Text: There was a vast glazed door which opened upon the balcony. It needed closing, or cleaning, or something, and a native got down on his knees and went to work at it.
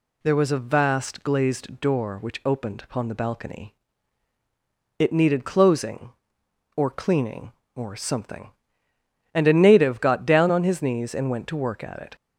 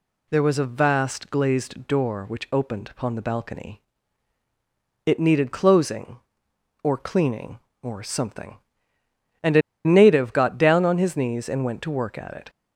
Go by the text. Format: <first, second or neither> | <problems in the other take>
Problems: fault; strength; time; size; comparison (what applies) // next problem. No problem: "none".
first | pauses between "a" and "native"; slight; at 9.6 s; 0.24 s long